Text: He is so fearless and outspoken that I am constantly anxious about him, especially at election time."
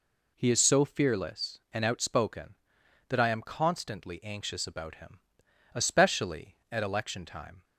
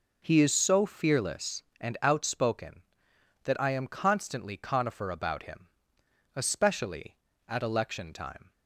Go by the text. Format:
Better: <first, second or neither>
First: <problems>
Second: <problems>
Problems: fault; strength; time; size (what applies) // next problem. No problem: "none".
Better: first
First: none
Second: says "conifer" for "anxious"; at 4.5 s